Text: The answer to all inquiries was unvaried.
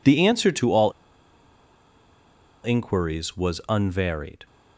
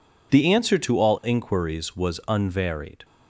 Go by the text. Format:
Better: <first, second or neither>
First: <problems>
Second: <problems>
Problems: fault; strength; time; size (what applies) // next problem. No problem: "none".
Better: second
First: pauses between "all" and "inquiries"; strong; at 0.9 s; 1.7 s long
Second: none